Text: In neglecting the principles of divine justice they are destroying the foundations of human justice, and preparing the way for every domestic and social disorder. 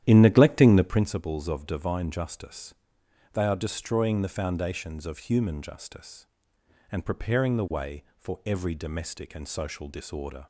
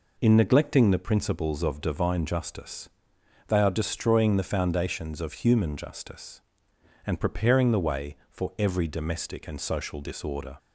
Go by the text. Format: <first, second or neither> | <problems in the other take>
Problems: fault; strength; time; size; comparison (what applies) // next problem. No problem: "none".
second | starts louder than the rest; strong; until 1.1 s; 11 dB // pauses between "justice" and "they"; noticeable; at 2.7 s; 0.58 s long; noticeable in the second